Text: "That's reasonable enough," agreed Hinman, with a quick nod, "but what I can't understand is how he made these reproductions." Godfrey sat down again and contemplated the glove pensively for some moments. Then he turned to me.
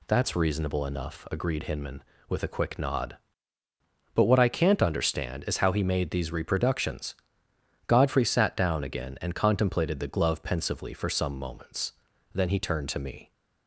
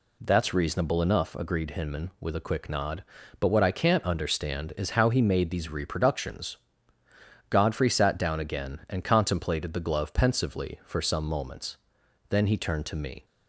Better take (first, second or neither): neither